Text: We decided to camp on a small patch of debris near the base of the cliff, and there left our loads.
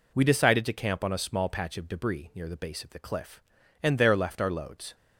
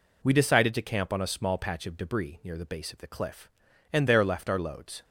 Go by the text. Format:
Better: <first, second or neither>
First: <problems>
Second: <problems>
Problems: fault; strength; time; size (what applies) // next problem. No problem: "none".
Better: neither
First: none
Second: none